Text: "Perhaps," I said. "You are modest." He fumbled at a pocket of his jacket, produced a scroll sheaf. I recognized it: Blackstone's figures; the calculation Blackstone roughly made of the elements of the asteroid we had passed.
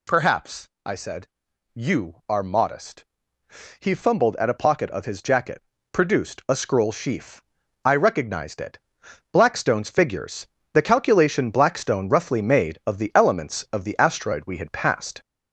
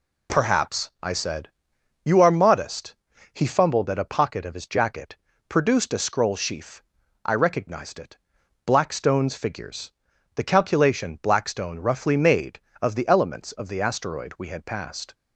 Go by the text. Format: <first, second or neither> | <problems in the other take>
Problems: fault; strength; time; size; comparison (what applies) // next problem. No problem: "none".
second | gets louder; noticeable; throughout; 4.5 dB